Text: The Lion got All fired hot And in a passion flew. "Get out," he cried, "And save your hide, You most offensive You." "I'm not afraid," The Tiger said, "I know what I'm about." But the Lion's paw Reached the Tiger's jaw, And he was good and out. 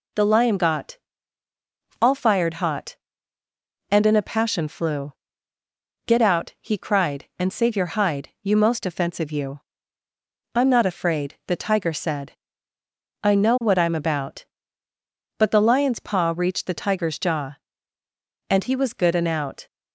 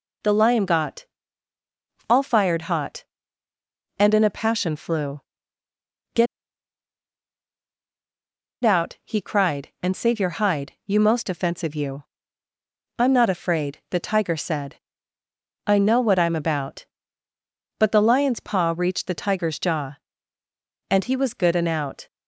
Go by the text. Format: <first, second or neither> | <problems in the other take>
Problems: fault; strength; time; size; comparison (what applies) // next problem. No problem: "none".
first | pauses between "got" and "All"; at 1.0 s; 1.0 s long; also in the first // pauses between "Get" and "out"; strong; at 6.2 s; 2.3 s long